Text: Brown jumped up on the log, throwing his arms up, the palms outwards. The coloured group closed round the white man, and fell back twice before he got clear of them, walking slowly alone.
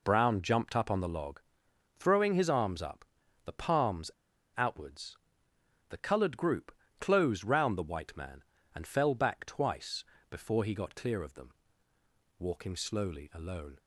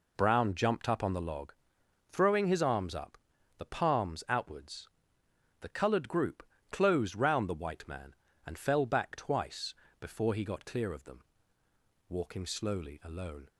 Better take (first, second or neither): second